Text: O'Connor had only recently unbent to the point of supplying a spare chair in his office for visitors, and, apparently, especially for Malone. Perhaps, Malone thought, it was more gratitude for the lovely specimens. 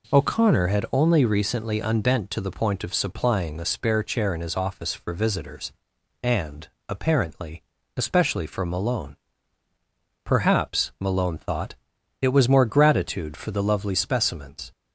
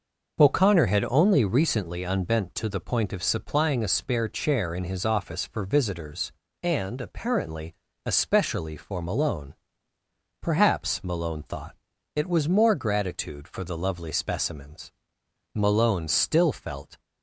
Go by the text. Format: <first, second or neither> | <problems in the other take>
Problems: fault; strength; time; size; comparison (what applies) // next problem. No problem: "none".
first | goes on to say "Malone still felt"; from 15.5 s on; 1.4 s long